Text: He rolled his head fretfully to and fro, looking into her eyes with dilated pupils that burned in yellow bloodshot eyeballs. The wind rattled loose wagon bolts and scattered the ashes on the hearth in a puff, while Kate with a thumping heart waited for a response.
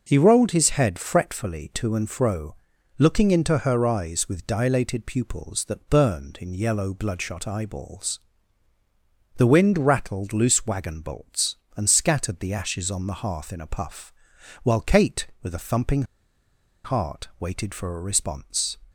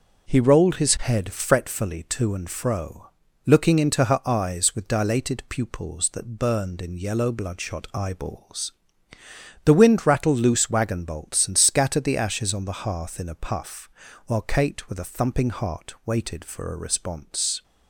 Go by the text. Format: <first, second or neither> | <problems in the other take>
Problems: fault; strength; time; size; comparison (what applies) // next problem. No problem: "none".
second | pauses between "thumping" and "heart"; noticeable; at 16.0 s; 0.81 s long